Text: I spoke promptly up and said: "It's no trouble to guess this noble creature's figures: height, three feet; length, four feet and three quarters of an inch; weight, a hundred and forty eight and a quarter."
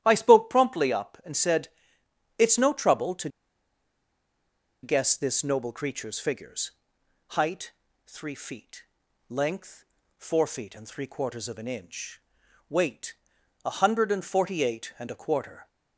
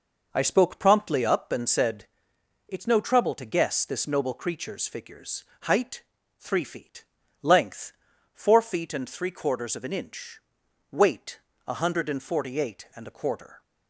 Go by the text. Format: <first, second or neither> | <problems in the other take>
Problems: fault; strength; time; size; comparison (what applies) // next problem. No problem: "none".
second | starts louder than the rest; strong; until 1.0 s; 12 dB // pauses between "to" and "guess"; strong; at 3.2 s; 1.5 s long